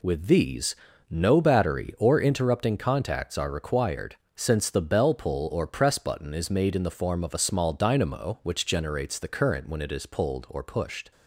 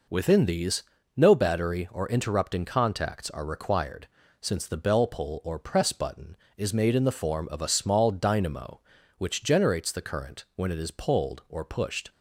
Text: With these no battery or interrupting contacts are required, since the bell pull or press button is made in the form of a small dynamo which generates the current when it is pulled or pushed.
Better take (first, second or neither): first